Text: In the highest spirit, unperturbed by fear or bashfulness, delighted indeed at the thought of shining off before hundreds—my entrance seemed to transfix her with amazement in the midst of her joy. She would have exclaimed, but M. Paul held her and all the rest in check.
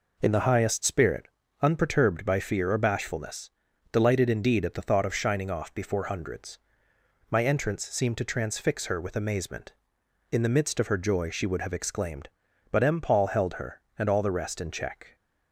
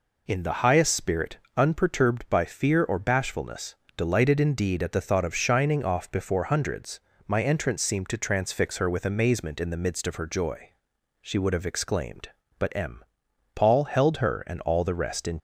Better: first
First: none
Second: stops before "check"; at 15.3 s

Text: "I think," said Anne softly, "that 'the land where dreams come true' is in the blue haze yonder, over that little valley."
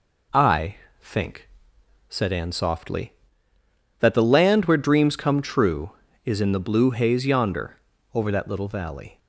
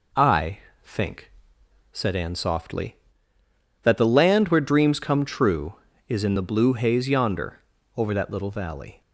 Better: neither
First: pauses between "I" and "think"; slight; at 0.7 s; 0.24 s long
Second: pauses between "I" and "think"; slight; at 0.5 s; 0.24 s long

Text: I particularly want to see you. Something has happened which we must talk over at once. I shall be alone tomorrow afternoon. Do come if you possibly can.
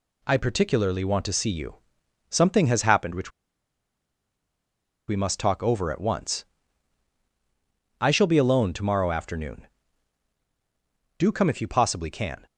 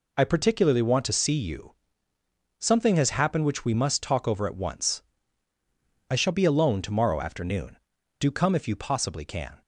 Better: second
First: pauses between "which" and "we"; strong; at 3.3 s; 1.7 s long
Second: none

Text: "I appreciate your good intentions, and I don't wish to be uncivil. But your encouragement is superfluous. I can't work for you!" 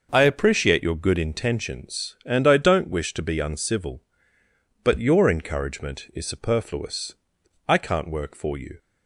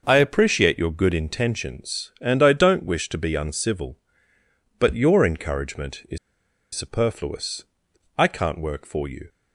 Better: first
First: starts louder than the rest; noticeable; until 1.1 s; 6 dB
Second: starts louder than the rest; noticeable; until 1.0 s; 6 dB // pauses between "is" and "superfluous"; noticeable; at 6.1 s; 0.56 s long

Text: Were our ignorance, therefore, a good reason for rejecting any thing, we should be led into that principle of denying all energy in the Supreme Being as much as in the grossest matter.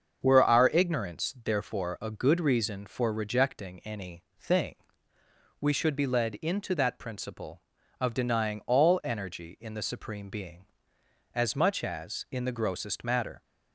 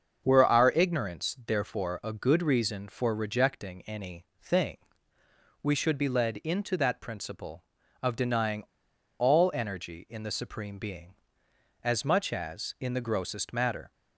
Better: first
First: starts louder than the rest; until 1.2 s; 6.5 dB // pauses between "any" and "thing"; slight; at 4.2 s; 0.16 s long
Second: starts louder than the rest; until 1.2 s; 6.5 dB // pauses between "any" and "thing"; slight; at 4.2 s; 0.16 s long // pauses between "denying" and "all"; noticeable; at 8.6 s; 0.54 s long

